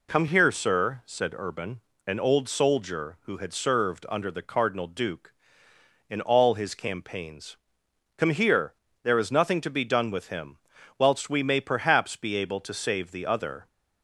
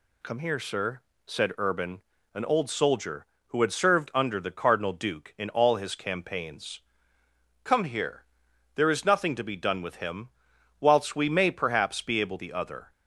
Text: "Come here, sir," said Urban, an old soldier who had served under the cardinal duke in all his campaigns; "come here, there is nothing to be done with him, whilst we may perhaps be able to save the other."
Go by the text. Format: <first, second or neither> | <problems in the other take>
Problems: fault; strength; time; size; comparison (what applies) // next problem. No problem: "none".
first | skips "to save"; at 12.3 s